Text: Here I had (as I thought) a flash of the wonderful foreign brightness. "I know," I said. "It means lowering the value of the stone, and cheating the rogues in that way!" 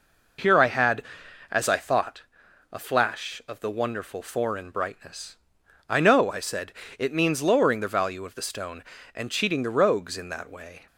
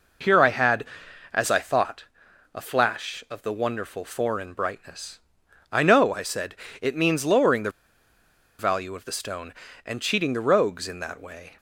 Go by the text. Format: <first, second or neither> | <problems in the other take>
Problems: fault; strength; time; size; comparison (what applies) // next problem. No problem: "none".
first | pauses between "the" and "value"; noticeable; at 7.7 s; 0.89 s long